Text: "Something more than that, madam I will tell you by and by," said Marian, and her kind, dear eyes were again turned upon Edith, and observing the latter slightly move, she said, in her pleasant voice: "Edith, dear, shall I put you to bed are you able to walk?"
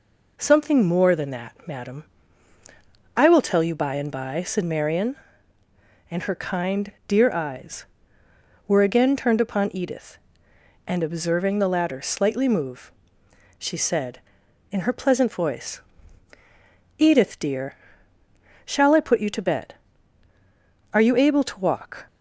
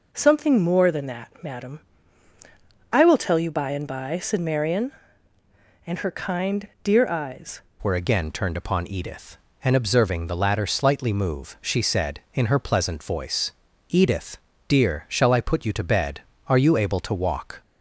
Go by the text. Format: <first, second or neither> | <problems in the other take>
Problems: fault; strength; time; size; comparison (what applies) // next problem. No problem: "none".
first | pauses between "madam" and "I"; at 1.8 s; 1.1 s long; also in the first // changes voice at "were"; from 7.8 s on; 9.8 s long